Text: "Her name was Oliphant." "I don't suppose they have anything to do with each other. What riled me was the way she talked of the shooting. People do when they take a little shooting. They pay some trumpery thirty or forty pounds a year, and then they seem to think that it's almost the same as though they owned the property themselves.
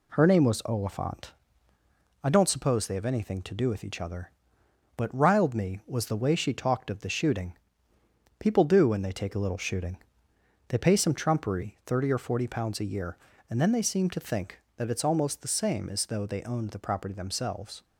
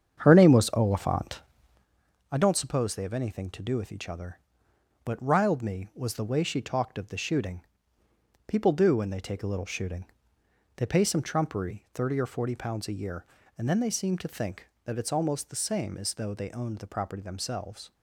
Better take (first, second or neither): first